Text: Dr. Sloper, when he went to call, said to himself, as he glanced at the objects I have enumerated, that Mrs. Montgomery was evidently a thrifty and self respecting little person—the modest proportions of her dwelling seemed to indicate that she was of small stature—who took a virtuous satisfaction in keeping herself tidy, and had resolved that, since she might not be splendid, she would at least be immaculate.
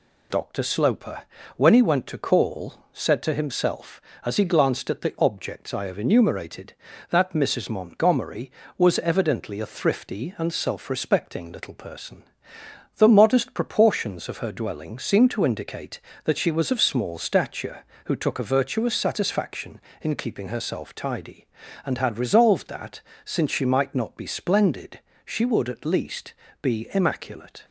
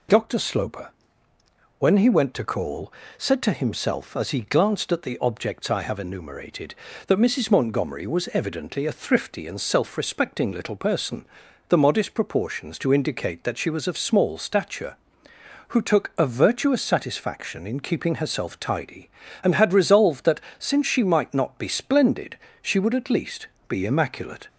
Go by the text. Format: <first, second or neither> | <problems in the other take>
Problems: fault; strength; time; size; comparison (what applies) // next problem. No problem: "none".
first | skips "of her dwelling seemed"; at 12.7 s // pauses between "least" and "be"; slight; at 23.4 s; 0.22 s long; slight in the first